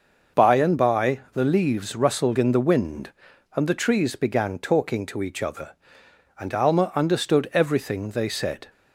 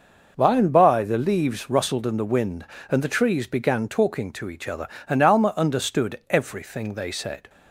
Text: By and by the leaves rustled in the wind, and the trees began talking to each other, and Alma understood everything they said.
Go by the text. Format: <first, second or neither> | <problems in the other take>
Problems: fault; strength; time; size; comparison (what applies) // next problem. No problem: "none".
neither | none